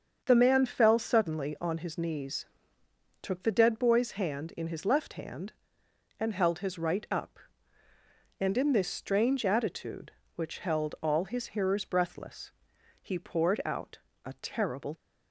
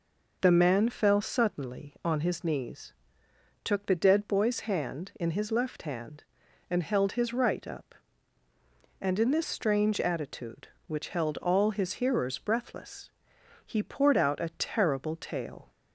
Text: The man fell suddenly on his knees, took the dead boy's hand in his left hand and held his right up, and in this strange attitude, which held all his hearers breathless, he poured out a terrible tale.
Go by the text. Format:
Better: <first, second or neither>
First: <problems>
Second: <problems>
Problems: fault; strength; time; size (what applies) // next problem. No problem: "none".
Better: second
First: starts louder than the rest; until 1.2 s; 7 dB // pauses between "out" and "a"; slight; at 13.9 s; 0.26 s long // stops before "tale"; at 14.9 s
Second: none